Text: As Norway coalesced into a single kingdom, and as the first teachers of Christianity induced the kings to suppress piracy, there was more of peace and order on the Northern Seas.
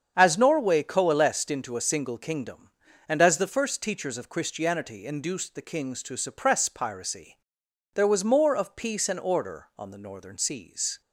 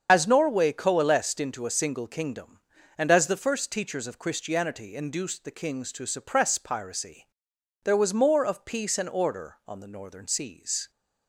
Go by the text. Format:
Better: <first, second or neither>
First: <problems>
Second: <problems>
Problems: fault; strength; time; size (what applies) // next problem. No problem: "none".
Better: first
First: starts louder than the rest; strong; until 1.1 s; 7.5 dB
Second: loses the start of "As"; at 0.0 s; 35 ms // starts louder than the rest; until 1.1 s; 7 dB